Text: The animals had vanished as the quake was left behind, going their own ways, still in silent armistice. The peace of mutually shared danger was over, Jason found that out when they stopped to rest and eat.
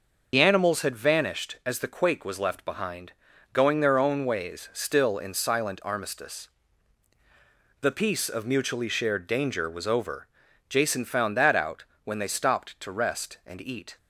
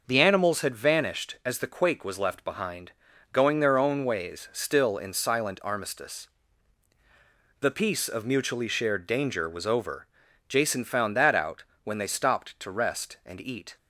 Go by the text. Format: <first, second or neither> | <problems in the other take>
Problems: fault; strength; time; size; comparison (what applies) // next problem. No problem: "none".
second | loses the start of "The"; at 0.3 s; 60 ms // starts louder than the rest; noticeable; until 1.3 s; 6 dB // pauses between "out" and "when"; slight; at 11.8 s; 0.22 s long; slight in the second